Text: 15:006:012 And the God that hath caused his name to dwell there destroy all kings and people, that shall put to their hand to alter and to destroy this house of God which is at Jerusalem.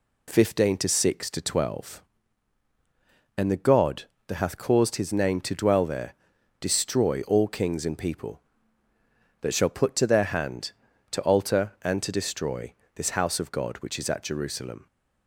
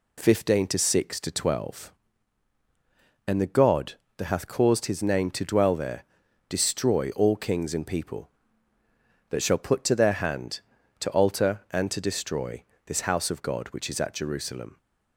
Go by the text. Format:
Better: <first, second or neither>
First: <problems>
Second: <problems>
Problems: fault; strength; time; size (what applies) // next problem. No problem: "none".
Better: neither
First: pauses between "there" and "destroy"; noticeable; at 6.1 s; 0.48 s long // pauses between "destroy" and "this"; slight; at 12.7 s; 0.23 s long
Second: pauses between "there" and "destroy"; noticeable; at 6.0 s; 0.46 s long // pauses between "destroy" and "this"; slight; at 12.6 s; 0.24 s long